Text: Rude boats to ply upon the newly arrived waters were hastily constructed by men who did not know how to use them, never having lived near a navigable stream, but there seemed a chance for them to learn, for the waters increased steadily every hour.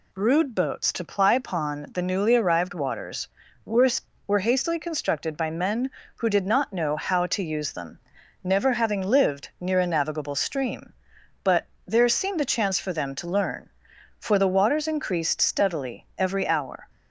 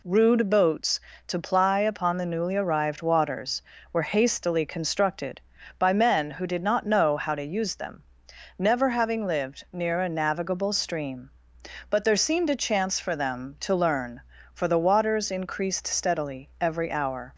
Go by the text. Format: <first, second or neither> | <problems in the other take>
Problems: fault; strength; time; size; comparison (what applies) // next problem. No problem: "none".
second | says "were" twice; at 4.2 s // pauses between "but" and "there"; slight; at 11.6 s; 0.20 s long